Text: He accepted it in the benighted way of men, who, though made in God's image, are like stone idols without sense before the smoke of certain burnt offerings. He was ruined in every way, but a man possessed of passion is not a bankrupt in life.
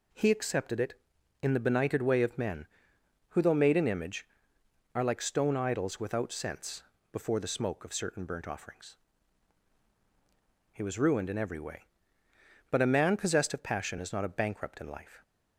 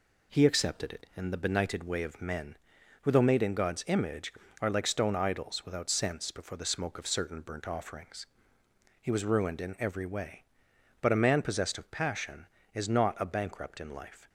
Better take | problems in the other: second | skips "God's"; at 3.8 s // pauses between "sense" and "before"; slight; at 6.8 s; 0.30 s long

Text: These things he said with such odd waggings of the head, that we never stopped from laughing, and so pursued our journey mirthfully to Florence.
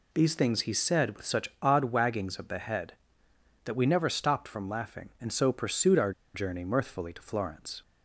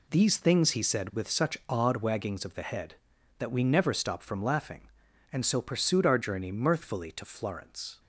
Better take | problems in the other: second | pauses between "our" and "journey"; slight; at 6.1 s; 0.23 s long

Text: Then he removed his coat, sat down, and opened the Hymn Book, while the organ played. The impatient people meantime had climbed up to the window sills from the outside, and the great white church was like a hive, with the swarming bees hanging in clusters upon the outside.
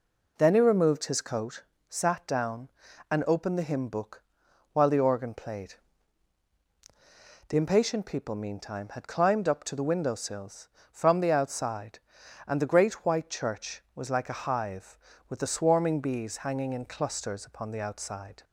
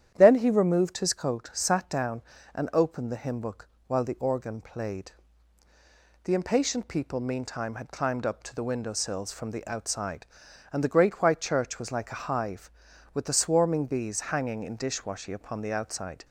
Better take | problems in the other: first | starts louder than the rest; strong; until 1.1 s; 10 dB // says "dishwashy" for "clusters"; at 14.7 s

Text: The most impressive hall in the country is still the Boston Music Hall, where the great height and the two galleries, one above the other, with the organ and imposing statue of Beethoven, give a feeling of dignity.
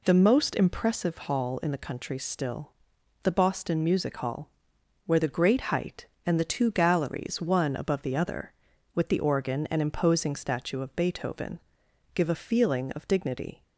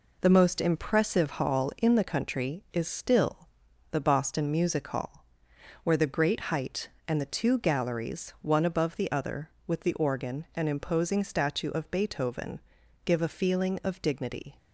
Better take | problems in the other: second | skips "is"; at 2.1 s // pauses between "still" and "the"; noticeable; at 2.7 s; 0.52 s long; also in the second

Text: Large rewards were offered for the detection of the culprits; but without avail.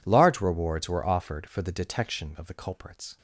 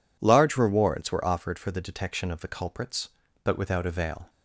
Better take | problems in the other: second | stops before "but without avail"; at 3.1 s

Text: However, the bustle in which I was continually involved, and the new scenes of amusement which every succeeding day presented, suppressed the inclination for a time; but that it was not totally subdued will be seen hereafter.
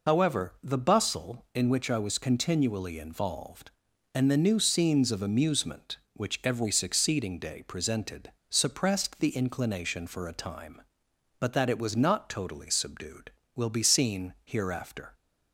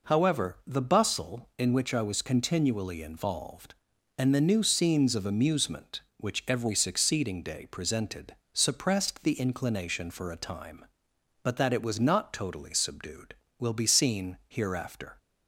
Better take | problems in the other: second | loses the start of "However"; at 0.0 s; 55 ms

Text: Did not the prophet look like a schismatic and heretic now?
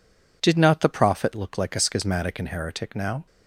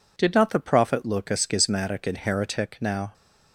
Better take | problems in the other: first | skips "like"; at 1.2 s

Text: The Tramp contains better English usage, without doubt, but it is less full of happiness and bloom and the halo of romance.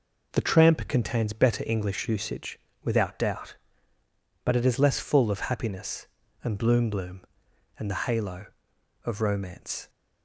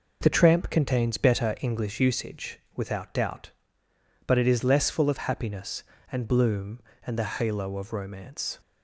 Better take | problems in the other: second | says "bloom" twice; at 6.8 s

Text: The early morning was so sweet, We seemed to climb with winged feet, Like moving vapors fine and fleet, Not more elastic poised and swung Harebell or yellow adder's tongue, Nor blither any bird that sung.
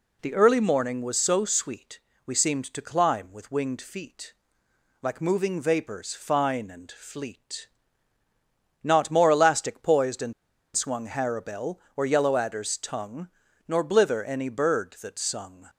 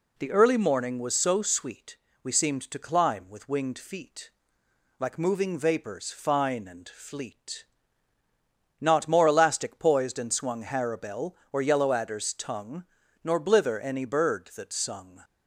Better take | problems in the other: second | pauses between "and" and "swung"; at 10.3 s; 0.42 s long

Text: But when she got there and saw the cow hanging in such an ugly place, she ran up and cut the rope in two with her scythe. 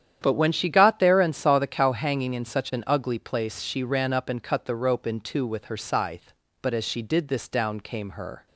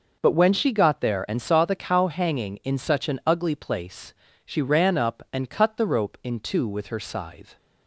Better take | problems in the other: second | starts louder than the rest; strong; until 1.2 s; 9.5 dB // goes on to say "But as she did this down came her"; strong; from 6.6 s on; 1.8 s long

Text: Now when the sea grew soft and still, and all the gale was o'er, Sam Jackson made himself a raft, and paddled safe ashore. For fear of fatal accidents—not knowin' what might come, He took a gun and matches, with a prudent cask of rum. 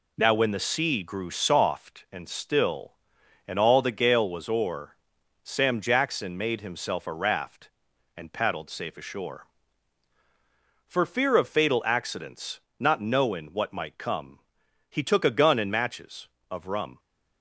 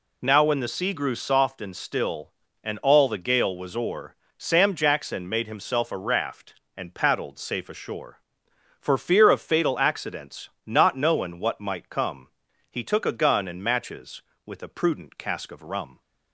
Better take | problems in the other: second | skips "with a prudent cask"; at 16.3 s

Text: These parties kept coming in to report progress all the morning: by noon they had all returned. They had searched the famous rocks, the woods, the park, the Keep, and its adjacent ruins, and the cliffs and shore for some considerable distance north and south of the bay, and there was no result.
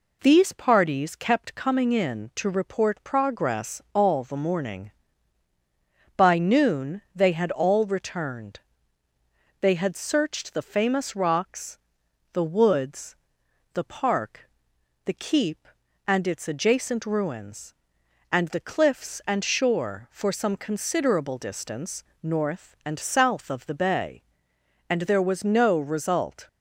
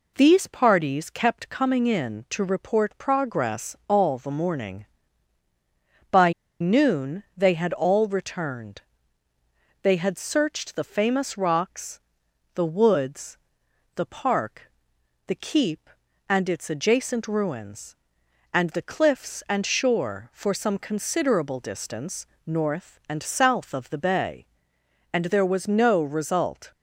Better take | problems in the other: first | pauses between "by" and "noon"; slight; at 6.3 s; 0.28 s long // pauses between "distance" and "north"; slight; at 22.2 s; 0.22 s long; slight in the first

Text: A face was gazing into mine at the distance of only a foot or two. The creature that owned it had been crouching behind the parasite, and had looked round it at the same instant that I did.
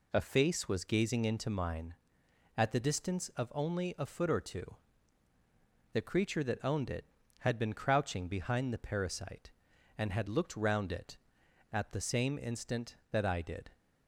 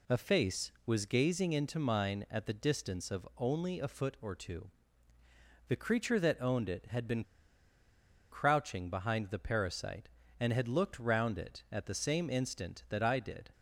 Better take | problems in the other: first | pauses between "been" and "crouching"; at 7.2 s; 1.0 s long

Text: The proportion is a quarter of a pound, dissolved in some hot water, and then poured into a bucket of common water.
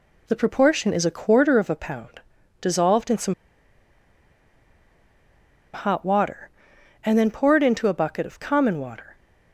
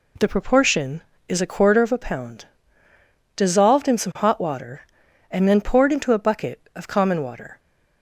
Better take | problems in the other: second | pauses between "some" and "hot"; strong; at 3.3 s; 2.3 s long

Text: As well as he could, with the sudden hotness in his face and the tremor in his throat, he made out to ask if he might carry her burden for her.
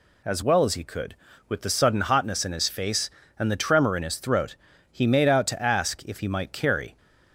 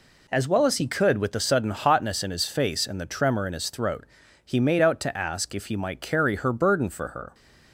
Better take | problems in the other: second | stops before "her burden for her"; at 6.9 s

